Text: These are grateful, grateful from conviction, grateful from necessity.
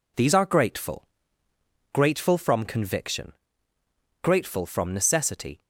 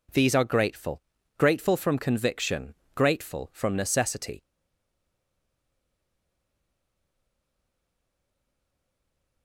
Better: first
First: none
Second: stays silent after the last word; strong; from 4.4 s on; 5.0 s long

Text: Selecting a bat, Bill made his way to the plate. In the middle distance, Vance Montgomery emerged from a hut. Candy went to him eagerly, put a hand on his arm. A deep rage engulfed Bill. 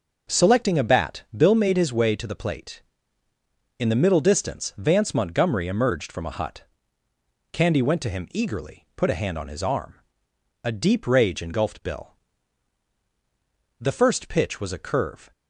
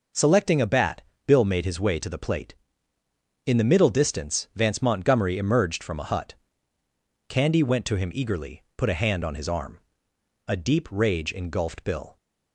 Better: second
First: goes on to say "The first pitch was a curve"; from 13.8 s on; 1.5 s long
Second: none

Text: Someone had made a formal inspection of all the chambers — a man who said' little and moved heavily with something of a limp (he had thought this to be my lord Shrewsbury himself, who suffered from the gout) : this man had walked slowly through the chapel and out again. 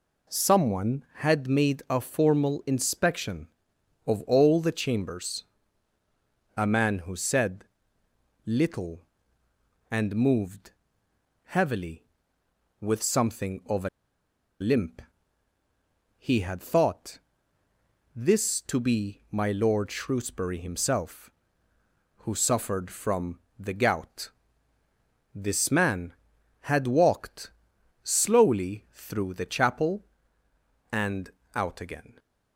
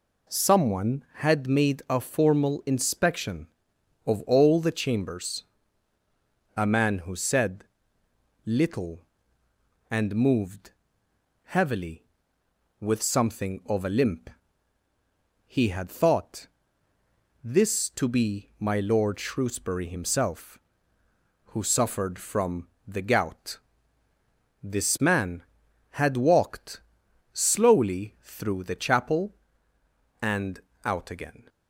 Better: second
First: pauses between "said" and "little"; noticeable; at 7.6 s; 0.82 s long // pauses between "moved" and "heavily"; noticeable; at 10.7 s; 0.74 s long // pauses between "a" and "limp"; noticeable; at 13.8 s; 0.71 s long // pauses between "thought" and "this"; noticeable; at 17.1 s; 0.94 s long // pauses between "from" and "the"; slight; at 23.3 s; 0.18 s long // pauses between "walked" and "slowly"; noticeable; at 27.5 s; 0.50 s long // pauses between "and" and "out"; slight; at 31.3 s; 0.24 s long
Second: pauses between "said" and "little"; noticeable; at 7.6 s; 0.82 s long // pauses between "moved" and "heavily"; noticeable; at 10.7 s; 0.74 s long // pauses between "thought" and "this"; noticeable; at 16.4 s; 0.94 s long // pauses between "from" and "the"; slight; at 22.6 s; 0.18 s long // pauses between "walked" and "slowly"; noticeable; at 26.8 s; 0.50 s long // pauses between "and" and "out"; slight; at 30.6 s; 0.24 s long

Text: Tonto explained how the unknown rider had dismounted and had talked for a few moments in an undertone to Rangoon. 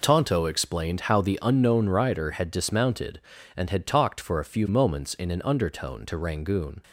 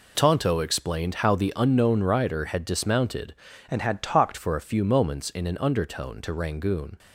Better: first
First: none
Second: changes voice from "and" to "talked"; from 3.7 to 4.3 s; 0.6 s long

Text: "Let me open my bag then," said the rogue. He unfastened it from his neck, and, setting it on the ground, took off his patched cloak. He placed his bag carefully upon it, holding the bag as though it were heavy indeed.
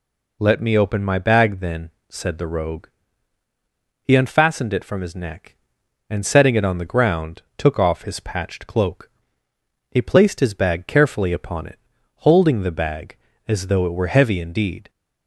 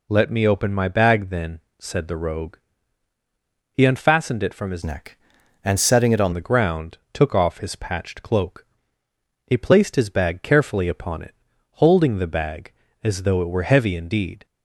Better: first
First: none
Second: changes voice from "neck" to "on"; from 4.8 to 6.3 s; 1.5 s long

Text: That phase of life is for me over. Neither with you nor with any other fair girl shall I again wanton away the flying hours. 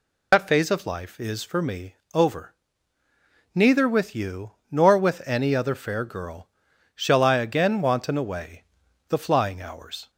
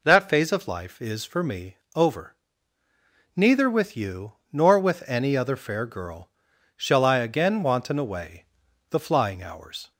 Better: second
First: loses the start of "That"; at 0.3 s; 105 ms // pauses between "me" and "over"; slight; at 1.9 s; 0.18 s long // pauses between "you" and "nor"; slight; at 4.5 s; 0.18 s long // pauses between "girl" and "shall"; noticeable; at 6.4 s; 0.46 s long // pauses between "away" and "the"; at 8.6 s; 0.44 s long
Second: pauses between "me" and "over"; slight; at 1.7 s; 0.18 s long // pauses between "you" and "nor"; slight; at 4.3 s; 0.18 s long // pauses between "girl" and "shall"; noticeable; at 6.2 s; 0.46 s long // pauses between "away" and "the"; at 8.4 s; 0.44 s long

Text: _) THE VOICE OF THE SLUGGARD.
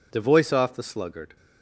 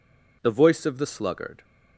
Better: second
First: says "Off" for "OF"; at 0.5 s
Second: none

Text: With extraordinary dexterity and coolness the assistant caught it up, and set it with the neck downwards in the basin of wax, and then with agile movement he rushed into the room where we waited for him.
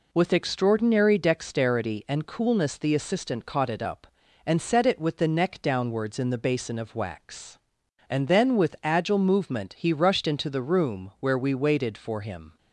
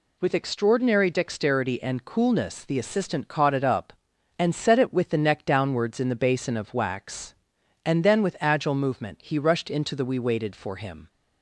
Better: first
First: none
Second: skips "room where"; at 10.0 s

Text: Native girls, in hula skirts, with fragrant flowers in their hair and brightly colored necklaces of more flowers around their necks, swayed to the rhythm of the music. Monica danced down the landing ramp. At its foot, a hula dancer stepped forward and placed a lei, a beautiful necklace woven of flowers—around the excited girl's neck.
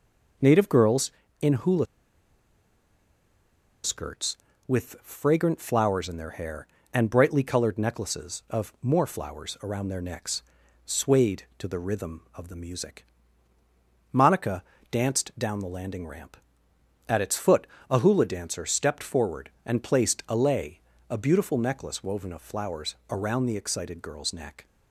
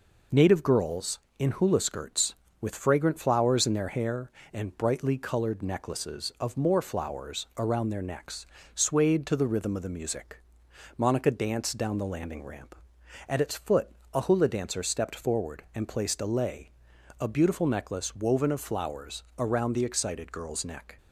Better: second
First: pauses between "hula" and "skirts"; strong; at 1.8 s; 1.9 s long // pauses between "Monica" and "danced"; slight; at 14.6 s; 0.28 s long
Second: none

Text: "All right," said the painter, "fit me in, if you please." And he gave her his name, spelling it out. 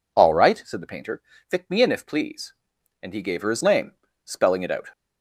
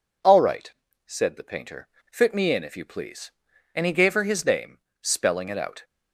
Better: second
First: skips "you"; at 2.0 s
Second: none

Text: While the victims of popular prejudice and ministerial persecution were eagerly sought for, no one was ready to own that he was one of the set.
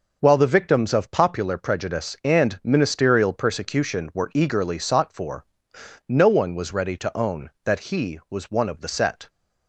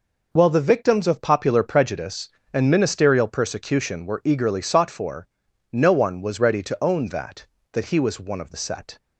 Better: first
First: none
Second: says "that" twice; at 7.7 s

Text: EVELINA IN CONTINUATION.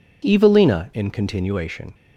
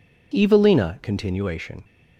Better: first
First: none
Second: skips "IN"; at 1.0 s

